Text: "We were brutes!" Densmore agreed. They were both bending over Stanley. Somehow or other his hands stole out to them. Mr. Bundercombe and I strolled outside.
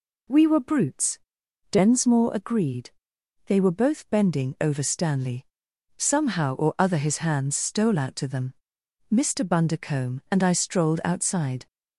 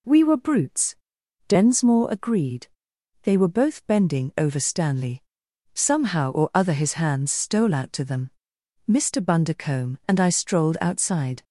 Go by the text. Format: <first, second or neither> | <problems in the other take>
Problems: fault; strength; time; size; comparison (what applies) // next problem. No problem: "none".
neither | none